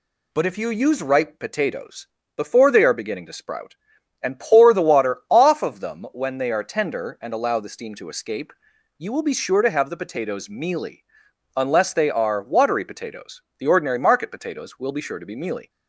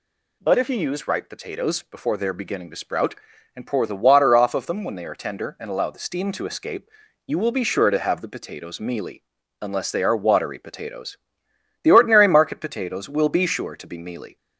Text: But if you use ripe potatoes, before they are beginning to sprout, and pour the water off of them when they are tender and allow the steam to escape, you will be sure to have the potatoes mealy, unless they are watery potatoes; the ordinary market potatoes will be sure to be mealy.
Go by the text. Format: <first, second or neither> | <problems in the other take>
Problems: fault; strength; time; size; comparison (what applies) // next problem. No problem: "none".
neither | none